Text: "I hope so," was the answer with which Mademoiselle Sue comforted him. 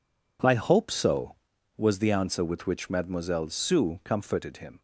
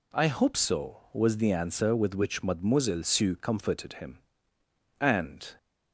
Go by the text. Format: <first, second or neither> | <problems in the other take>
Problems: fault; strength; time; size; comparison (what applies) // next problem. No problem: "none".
first | goes on to say "And"; from 4.9 s on; 0.56 s long